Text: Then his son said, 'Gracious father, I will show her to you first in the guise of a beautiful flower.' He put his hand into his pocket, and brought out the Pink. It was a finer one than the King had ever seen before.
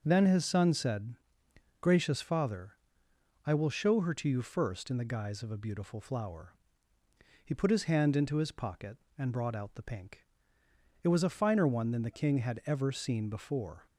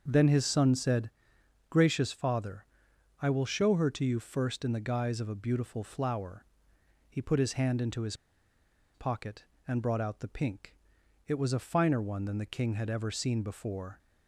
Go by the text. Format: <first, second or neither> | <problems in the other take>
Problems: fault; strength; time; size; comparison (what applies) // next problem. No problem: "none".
first | starts louder than the rest; until 1.0 s; 6.5 dB // pauses between "his" and "pocket"; noticeable; at 8.1 s; 0.79 s long